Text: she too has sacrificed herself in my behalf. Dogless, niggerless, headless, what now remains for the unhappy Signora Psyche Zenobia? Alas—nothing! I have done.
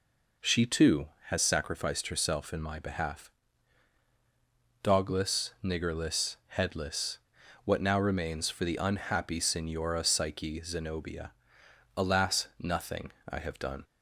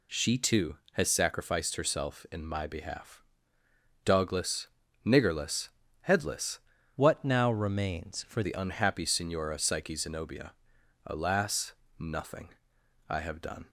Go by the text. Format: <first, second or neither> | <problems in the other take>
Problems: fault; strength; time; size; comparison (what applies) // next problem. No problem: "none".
first | changes voice from "what" to "for"; from 6.9 to 8.4 s; 1.5 s long